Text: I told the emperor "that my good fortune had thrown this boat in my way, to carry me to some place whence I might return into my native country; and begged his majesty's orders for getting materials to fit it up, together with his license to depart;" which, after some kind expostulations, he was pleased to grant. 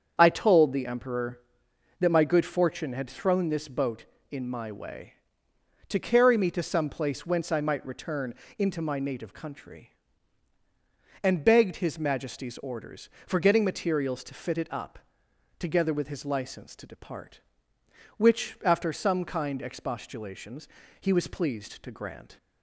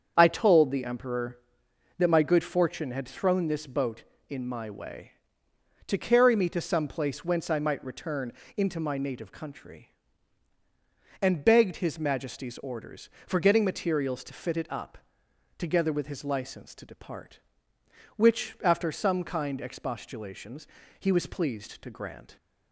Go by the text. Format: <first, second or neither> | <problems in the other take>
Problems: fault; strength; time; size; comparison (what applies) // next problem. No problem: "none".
neither | starts louder than the rest; the same in both // pauses between "return" and "into"; slight; the same in both